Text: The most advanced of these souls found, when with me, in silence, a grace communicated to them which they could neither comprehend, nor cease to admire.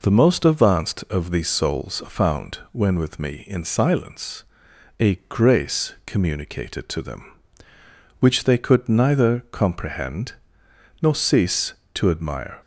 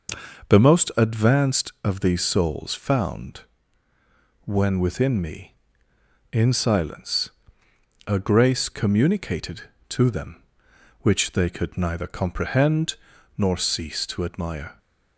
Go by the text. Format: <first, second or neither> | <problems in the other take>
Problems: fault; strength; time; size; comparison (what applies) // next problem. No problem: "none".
first | says "within" for "with"; at 4.8 s